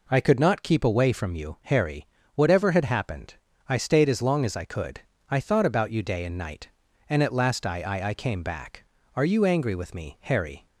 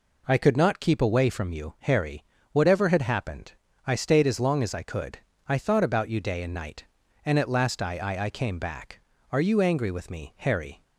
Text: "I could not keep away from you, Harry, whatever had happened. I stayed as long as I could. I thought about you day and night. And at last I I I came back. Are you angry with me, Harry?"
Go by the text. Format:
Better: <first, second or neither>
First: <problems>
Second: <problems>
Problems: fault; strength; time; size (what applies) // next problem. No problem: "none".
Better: neither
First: none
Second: none